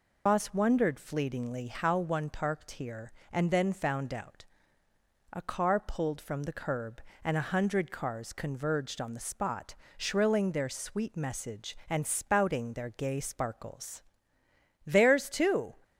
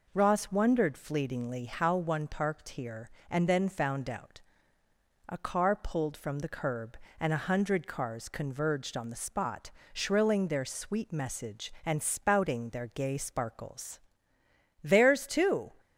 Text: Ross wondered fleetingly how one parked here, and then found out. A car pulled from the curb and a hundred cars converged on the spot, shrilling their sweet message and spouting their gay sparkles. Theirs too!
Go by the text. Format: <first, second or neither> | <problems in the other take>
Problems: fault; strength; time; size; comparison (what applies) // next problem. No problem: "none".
second | loses the start of "Ross"; at 0.2 s; 155 ms